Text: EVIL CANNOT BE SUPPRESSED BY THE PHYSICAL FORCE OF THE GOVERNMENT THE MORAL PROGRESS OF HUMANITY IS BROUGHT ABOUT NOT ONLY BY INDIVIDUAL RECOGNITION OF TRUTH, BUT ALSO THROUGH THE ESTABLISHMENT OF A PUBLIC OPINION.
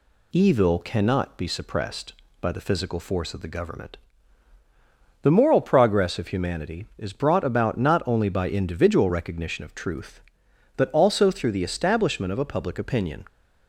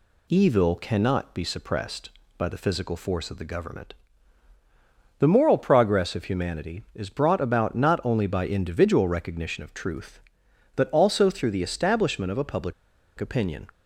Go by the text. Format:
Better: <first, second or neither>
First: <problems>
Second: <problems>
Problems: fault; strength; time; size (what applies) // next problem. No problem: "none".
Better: first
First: pauses between "GOVERNMENT" and "THE"; strong; at 3.9 s; 1.2 s long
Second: pauses between "GOVERNMENT" and "THE"; strong; at 3.9 s; 1.2 s long // pauses between "PUBLIC" and "OPINION"; at 12.7 s; 0.45 s long